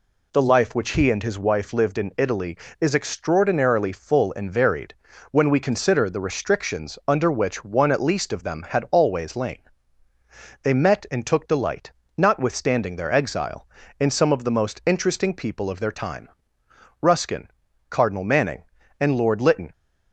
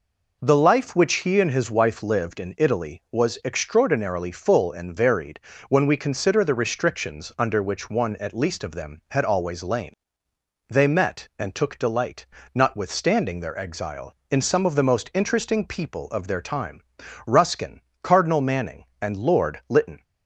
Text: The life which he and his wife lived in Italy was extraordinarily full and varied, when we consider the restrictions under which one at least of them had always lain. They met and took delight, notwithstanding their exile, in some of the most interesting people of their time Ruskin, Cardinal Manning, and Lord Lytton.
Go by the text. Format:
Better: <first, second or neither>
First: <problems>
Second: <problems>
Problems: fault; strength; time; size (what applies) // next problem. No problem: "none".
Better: second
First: says "is" for "was"; at 2.8 s // pauses between "time" and "Ruskin"; noticeable; at 16.2 s; 0.74 s long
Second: pauses between "time" and "Ruskin"; at 16.8 s; 0.44 s long